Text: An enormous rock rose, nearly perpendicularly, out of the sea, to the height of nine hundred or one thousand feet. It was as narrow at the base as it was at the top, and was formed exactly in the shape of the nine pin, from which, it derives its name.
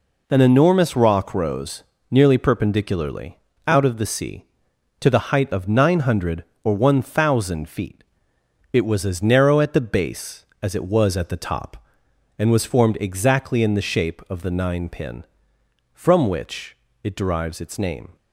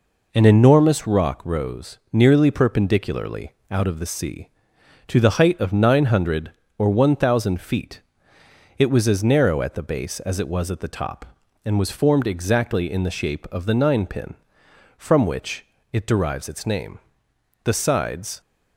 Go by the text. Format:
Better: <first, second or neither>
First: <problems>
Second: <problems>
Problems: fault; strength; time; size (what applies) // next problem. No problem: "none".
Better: first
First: none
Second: goes on to say "The sides"; noticeable; from 17.6 s on; 0.76 s long